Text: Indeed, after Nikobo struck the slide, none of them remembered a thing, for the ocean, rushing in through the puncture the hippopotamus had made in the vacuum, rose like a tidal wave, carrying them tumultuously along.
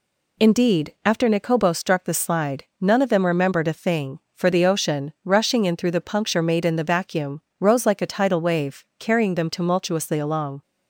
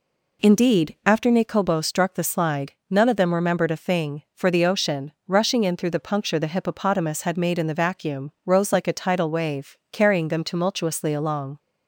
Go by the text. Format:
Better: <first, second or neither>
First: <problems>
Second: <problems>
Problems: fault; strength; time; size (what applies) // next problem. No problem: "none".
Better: second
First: skips "the hippopotamus had"; at 6.4 s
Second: none